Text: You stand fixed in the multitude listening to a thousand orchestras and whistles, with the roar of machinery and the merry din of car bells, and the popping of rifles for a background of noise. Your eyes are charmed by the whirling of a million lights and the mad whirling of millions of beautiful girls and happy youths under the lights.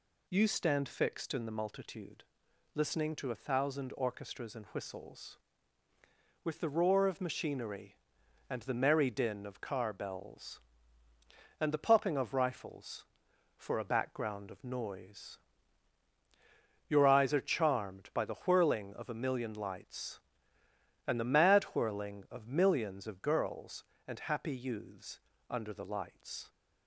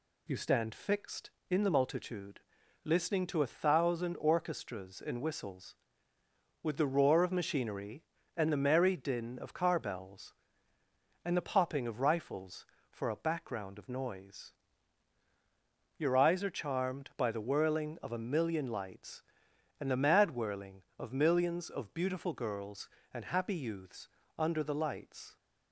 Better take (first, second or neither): second